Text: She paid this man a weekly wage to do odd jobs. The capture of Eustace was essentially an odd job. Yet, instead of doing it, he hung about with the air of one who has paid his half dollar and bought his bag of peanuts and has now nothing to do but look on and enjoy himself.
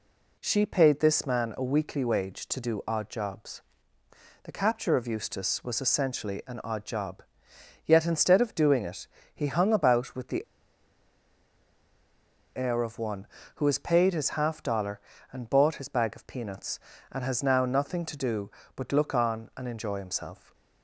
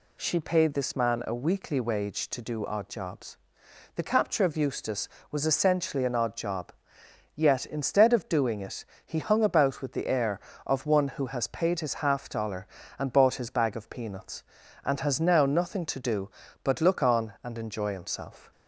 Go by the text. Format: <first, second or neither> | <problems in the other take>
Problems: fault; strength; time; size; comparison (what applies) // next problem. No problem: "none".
second | pauses between "the" and "air"; strong; at 10.4 s; 2.1 s long